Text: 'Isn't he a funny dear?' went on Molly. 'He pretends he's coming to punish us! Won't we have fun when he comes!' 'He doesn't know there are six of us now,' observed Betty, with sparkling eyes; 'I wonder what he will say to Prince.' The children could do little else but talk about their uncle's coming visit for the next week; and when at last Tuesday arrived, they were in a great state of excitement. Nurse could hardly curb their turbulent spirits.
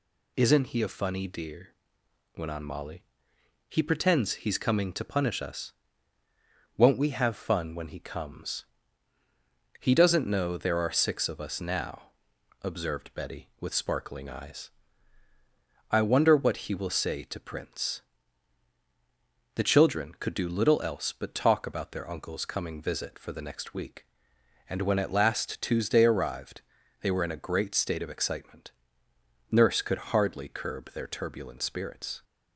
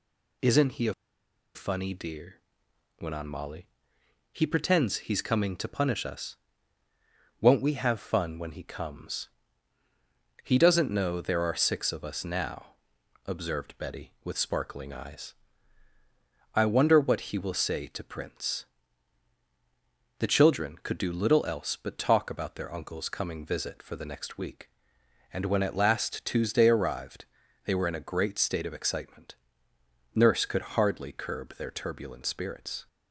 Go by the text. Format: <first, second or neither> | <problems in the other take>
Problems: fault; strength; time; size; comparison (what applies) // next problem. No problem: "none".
first | pauses between "a" and "funny"; noticeable; at 0.9 s; 0.61 s long